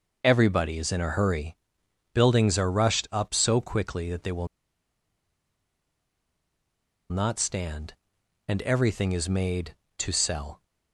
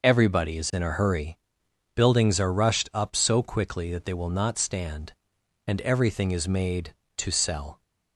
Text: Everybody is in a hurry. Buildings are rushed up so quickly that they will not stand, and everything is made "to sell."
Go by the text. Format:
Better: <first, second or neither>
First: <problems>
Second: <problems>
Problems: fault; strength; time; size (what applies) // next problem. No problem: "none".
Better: second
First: pauses between "will" and "not"; strong; at 4.4 s; 2.6 s long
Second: none